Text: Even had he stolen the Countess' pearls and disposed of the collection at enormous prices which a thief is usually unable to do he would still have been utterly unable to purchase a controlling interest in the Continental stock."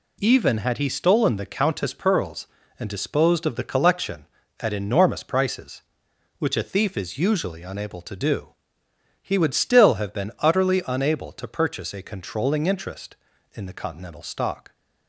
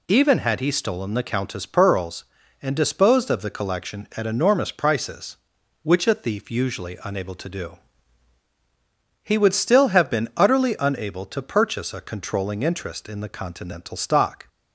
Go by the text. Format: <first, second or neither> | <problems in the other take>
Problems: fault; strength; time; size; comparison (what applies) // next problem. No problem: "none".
first | skips "is"; at 6.4 s // pauses between "do" and "he"; strong; at 7.7 s; 1.4 s long; noticeable in the first